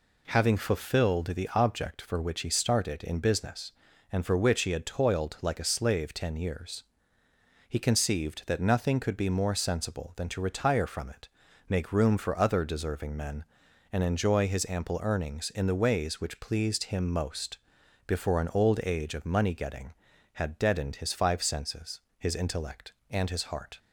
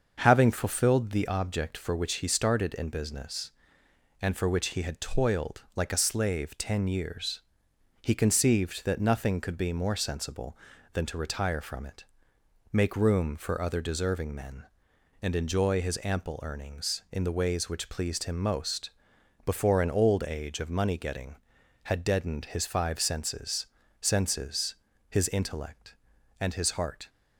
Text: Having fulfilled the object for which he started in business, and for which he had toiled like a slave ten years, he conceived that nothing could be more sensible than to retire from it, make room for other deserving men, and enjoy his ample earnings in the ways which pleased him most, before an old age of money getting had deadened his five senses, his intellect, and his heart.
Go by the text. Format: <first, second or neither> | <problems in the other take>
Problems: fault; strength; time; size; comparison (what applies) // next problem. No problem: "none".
first | starts louder than the rest; until 1.2 s; 6.5 dB // says "senses" twice; at 24.0 s